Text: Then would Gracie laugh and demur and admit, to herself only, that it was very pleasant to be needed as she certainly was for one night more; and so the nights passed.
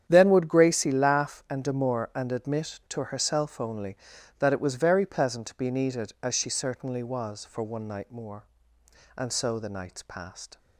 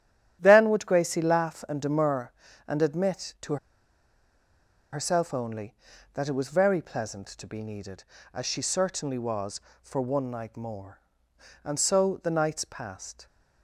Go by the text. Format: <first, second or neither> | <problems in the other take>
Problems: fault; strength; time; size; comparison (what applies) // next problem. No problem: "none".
first | starts louder than the rest; strong; until 1.4 s; 11.5 dB; strong in the first // pauses between "to" and "herself"; strong; at 3.5 s; 1.3 s long